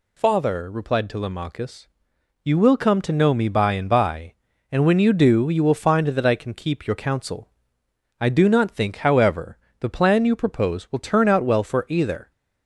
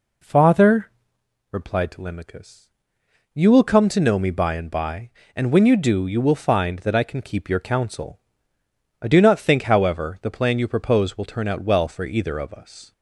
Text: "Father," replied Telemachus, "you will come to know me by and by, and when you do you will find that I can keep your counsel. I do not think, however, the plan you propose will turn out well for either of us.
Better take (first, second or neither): second